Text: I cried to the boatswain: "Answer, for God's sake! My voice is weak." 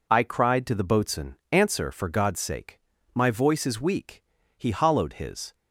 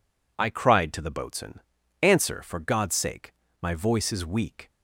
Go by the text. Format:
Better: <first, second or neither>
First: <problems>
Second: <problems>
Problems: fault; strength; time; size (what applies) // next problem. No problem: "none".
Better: second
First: goes on to say "He hollowed his"; noticeable; from 4.5 s on; 0.98 s long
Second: none